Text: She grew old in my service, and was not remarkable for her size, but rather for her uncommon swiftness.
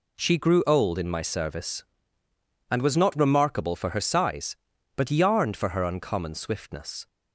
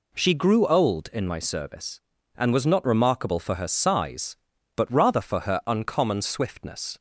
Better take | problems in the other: second | says "yarned" for "rather"; at 5.1 s

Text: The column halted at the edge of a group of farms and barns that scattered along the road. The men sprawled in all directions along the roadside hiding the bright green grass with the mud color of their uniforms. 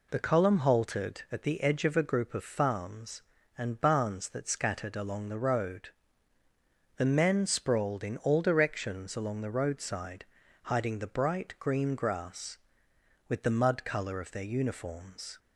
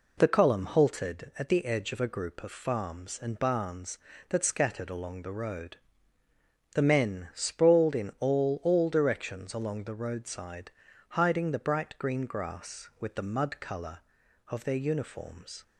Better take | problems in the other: first | says "all" twice; at 8.6 s // pauses between "roadside" and "hiding"; at 10.7 s; 0.38 s long; also in the first

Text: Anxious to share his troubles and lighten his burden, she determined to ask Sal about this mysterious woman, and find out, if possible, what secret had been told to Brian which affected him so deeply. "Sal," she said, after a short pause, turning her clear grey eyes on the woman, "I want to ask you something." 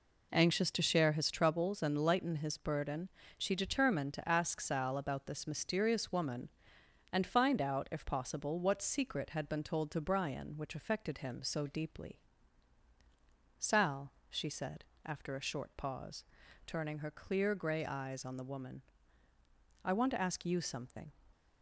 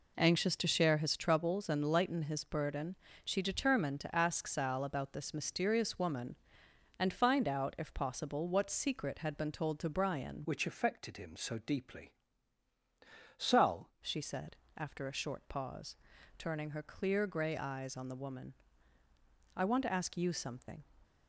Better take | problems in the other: first | changes voice from "which" to "Sal"; from 10.4 to 13.9 s; 3.5 s long

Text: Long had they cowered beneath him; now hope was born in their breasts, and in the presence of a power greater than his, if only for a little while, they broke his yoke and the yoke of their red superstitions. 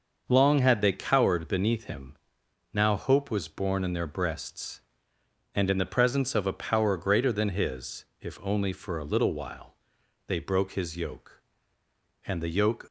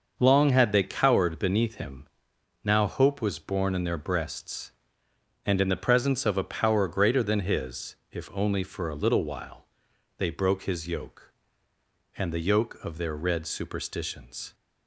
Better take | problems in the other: second | starts louder than the rest; until 1.3 s; 6 dB; also in the second // stops before "of their red superstitions"; at 12.8 s

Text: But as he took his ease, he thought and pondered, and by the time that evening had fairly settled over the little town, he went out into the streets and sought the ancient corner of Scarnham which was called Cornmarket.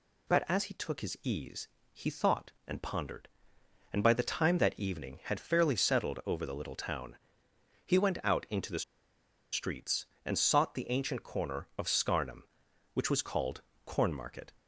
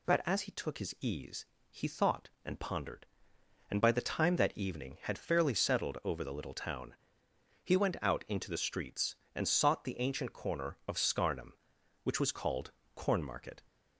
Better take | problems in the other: second | pauses between "the" and "streets"; noticeable; at 8.8 s; 0.70 s long // pauses between "called" and "Cornmarket"; slight; at 13.6 s; 0.26 s long; slight in the second

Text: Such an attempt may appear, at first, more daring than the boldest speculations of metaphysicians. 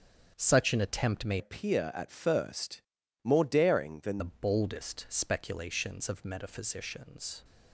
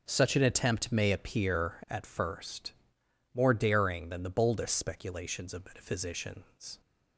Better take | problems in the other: second | starts louder than the rest; strong; until 1.3 s; 7.5 dB // changes voice from "appear" to "than"; from 1.3 to 4.1 s; 2.8 s long

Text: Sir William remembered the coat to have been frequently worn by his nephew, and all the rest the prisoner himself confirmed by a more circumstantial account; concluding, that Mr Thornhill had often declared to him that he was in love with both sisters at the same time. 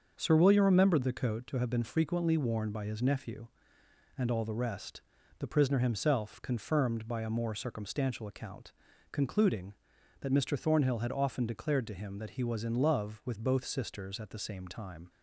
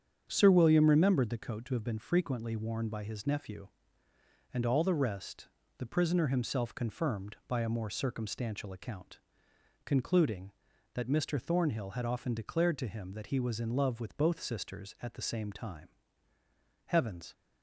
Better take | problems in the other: first | starts louder than the rest; strong; until 1.3 s; 8 dB; also in the first // pauses between "rest" and "the"; slight; at 5.4 s; 0.30 s long; also in the first // goes on to say "Heavens"; slight; from 16.8 s on; 0.46 s long

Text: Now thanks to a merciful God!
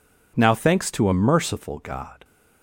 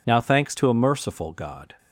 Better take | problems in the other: neither | none

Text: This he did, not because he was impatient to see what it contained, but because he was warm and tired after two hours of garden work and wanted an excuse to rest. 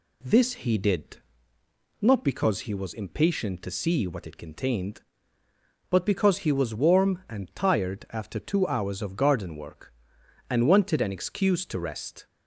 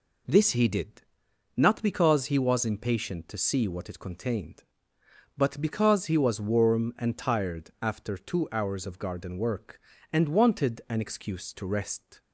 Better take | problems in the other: neither | none

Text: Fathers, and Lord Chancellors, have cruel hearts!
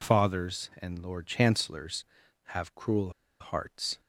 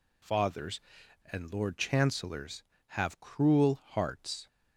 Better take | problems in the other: second | pauses between "cruel" and "hearts"; slight; at 3.1 s; 0.30 s long

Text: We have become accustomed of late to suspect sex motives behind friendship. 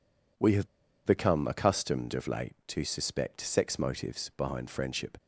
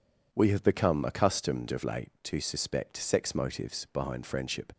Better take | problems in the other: second | pauses between "have" and "become"; at 0.6 s; 0.38 s long

